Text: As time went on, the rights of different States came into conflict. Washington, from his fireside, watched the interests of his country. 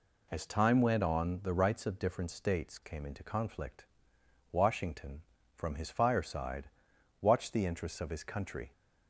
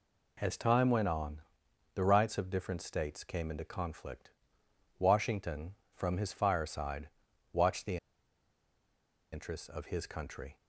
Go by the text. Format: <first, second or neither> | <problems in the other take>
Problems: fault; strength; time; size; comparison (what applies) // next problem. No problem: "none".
first | pauses between "the" and "interests"; strong; at 7.9 s; 1.3 s long